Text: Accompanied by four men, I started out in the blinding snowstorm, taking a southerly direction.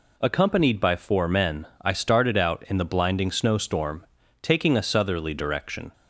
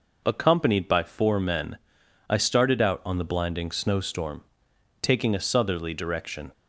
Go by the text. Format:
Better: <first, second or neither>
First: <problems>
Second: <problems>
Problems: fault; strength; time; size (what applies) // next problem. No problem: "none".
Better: first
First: none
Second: says "on" for "in"; at 3.0 s